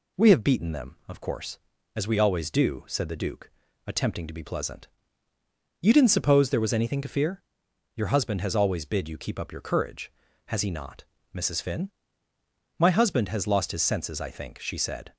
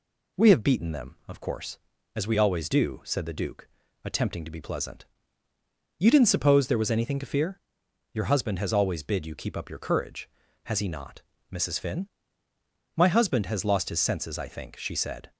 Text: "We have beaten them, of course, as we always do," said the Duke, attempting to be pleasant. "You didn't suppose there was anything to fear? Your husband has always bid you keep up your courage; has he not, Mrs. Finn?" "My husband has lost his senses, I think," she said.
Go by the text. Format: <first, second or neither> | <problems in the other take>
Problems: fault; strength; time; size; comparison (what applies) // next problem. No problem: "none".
neither | none